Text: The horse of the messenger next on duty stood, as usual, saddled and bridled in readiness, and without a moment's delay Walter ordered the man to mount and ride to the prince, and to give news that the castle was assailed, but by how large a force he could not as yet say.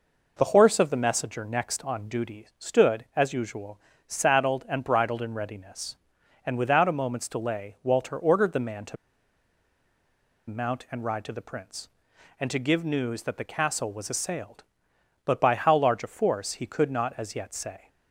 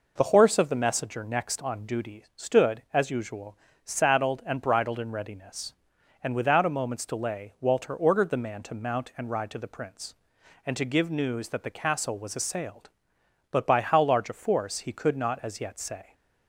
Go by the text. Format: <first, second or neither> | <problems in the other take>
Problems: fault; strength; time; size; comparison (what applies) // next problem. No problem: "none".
second | pauses between "to" and "mount"; strong; at 8.9 s; 1.5 s long